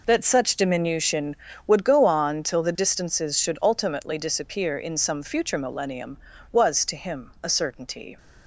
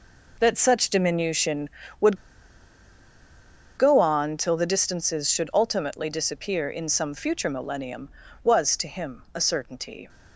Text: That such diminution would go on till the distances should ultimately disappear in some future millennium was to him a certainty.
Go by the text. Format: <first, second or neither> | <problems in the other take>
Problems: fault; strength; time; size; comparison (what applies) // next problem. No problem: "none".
first | pauses between "would" and "go"; strong; at 2.1 s; 1.6 s long